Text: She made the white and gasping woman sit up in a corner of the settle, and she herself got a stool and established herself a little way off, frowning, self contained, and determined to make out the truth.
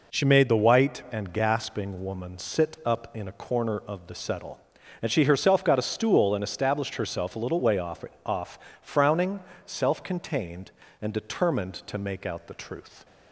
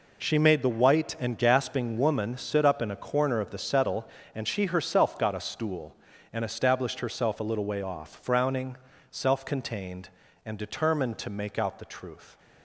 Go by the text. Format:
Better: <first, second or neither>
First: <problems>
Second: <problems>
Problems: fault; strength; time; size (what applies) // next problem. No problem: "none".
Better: second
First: says "off" twice; at 8.2 s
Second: none